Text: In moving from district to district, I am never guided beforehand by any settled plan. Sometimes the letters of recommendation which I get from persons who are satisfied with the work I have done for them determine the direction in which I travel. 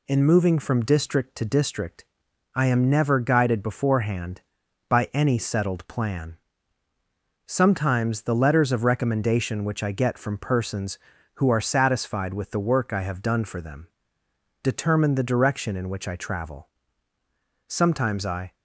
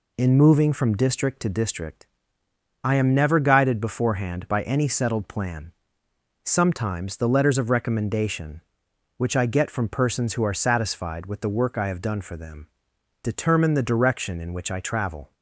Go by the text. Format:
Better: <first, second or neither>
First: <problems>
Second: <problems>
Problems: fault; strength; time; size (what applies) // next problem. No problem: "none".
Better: second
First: pauses between "them" and "determine"; noticeable; at 13.8 s; 0.74 s long // goes on to say "Sometimes I"; noticeable; from 17.6 s on; 0.86 s long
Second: pauses between "them" and "determine"; noticeable; at 12.6 s; 0.54 s long